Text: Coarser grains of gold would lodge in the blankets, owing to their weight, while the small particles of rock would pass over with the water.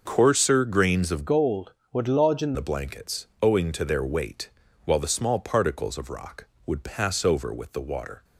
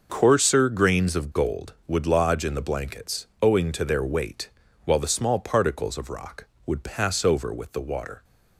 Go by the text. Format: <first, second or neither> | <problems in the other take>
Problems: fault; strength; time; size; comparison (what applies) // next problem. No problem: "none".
second | changes voice from "gold" to "in"; from 1.2 to 2.5 s; 1.3 s long